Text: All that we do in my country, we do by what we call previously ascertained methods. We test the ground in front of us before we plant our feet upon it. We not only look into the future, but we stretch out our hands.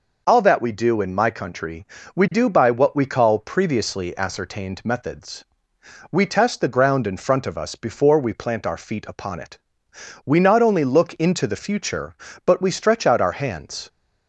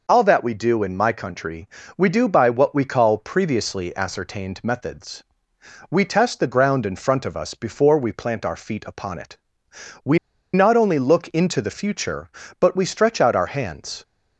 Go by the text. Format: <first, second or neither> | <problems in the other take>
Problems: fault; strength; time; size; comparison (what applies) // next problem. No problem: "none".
first | pauses between "We" and "not"; slight; at 10.1 s; 0.36 s long